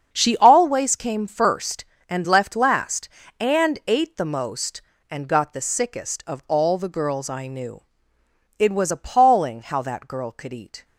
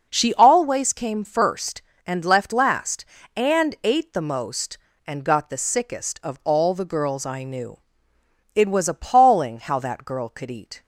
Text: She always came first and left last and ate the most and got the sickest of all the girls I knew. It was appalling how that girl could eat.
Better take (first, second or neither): second